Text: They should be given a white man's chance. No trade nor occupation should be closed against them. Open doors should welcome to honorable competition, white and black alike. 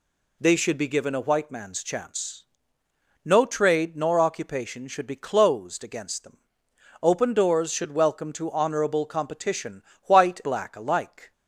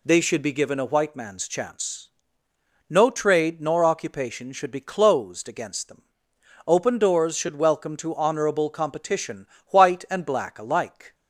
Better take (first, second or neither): second